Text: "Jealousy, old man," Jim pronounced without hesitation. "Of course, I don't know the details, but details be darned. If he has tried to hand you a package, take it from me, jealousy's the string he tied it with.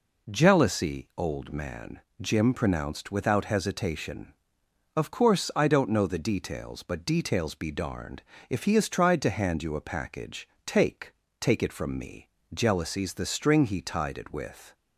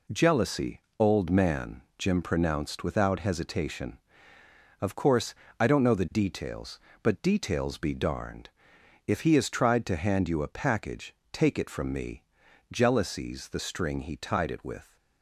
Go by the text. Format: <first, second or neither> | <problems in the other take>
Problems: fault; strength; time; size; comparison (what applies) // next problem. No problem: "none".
second | says "take" twice; at 11.3 s